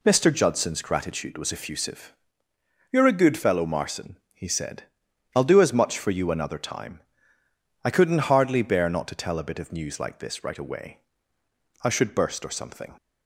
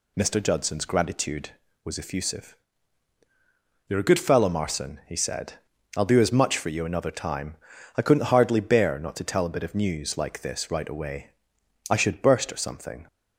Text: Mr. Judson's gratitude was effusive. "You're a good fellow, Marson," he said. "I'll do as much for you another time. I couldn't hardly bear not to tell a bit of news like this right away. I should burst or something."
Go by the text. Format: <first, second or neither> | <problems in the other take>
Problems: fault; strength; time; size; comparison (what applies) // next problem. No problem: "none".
neither | none